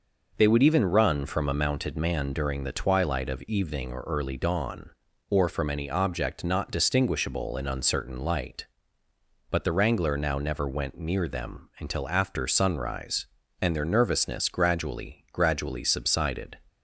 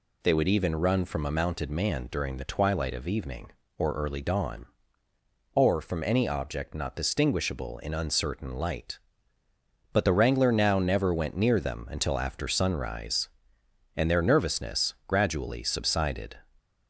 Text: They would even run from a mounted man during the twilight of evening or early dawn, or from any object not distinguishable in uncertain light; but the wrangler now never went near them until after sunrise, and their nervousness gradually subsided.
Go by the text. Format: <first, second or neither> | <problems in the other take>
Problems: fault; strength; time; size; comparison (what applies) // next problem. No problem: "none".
second | says "gradually" twice; at 15.3 s